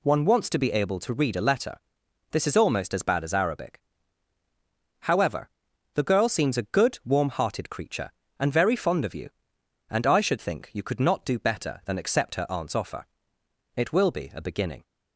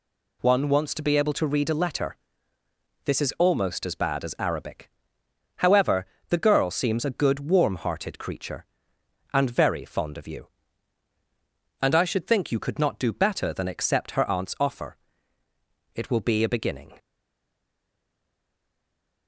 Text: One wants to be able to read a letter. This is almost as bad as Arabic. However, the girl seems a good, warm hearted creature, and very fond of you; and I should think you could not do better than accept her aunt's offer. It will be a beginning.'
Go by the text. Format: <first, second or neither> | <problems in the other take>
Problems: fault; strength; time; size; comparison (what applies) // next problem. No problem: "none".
first | stays silent after the last word; from 16.9 s on; 2.3 s long